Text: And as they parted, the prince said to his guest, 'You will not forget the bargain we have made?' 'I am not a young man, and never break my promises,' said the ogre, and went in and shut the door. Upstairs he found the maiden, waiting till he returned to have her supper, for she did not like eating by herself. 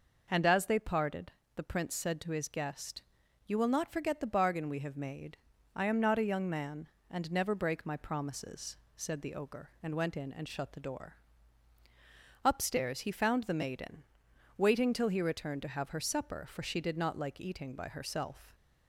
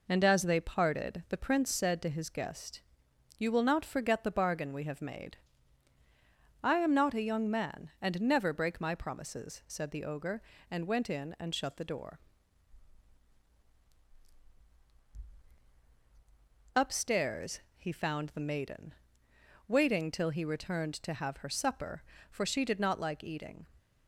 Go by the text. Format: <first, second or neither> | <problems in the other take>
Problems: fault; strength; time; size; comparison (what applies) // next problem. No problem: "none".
first | pauses between "Upstairs" and "he"; slight; at 17.5 s; 0.16 s long // stops before "by herself"; at 23.7 s